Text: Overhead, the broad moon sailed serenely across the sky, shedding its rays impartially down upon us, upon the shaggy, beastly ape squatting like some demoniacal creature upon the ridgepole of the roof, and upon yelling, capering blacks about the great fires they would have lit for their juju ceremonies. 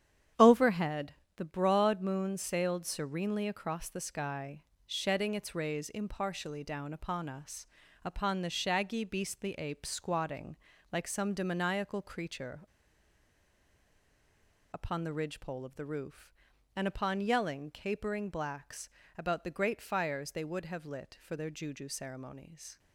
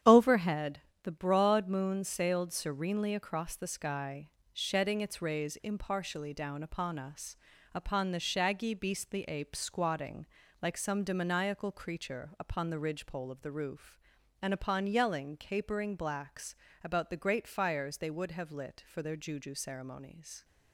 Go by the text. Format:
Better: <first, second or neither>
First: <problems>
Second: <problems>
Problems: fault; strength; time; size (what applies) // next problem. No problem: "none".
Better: second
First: starts louder than the rest; strong; until 1.6 s; 9.5 dB // pauses between "squatting" and "like"; slight; at 10.5 s; 0.34 s long // pauses between "creature" and "upon"; strong; at 12.6 s; 2.0 s long // pauses between "blacks" and "about"; slight; at 18.8 s; 0.28 s long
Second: starts louder than the rest; strong; until 1.2 s; 9.5 dB // pauses between "squatting" and "like"; slight; at 10.2 s; 0.34 s long // pauses between "blacks" and "about"; slight; at 16.5 s; 0.28 s long